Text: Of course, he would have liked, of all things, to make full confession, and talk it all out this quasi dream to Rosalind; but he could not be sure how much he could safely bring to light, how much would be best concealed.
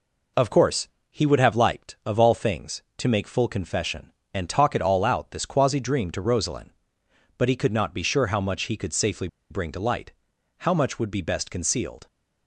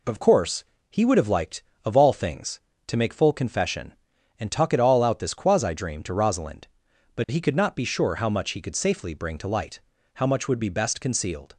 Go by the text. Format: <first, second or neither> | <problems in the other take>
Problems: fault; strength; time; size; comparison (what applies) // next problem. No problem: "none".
second | pauses between "safely" and "bring"; slight; at 9.2 s; 0.22 s long